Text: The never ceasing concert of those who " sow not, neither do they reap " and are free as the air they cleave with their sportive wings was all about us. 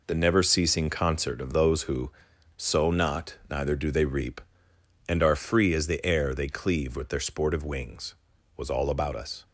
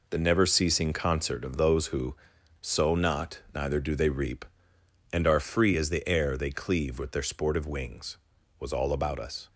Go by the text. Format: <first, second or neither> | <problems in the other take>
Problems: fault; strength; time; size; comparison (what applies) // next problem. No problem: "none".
neither | none